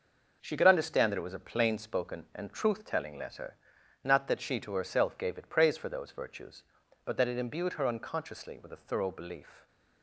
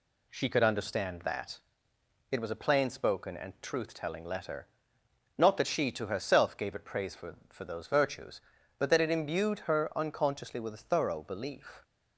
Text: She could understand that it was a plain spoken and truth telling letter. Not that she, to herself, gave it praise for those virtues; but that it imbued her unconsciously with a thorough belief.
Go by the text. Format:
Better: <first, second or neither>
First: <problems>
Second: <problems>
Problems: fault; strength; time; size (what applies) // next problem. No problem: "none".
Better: first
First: none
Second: pauses between "that" and "it"; noticeable; at 1.5 s; 0.72 s long // says "for" twice; at 7.4 s